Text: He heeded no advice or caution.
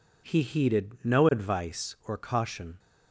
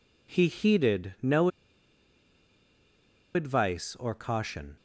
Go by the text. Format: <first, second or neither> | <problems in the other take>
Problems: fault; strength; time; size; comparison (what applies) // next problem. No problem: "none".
first | pauses between "no" and "advice"; strong; at 1.4 s; 1.8 s long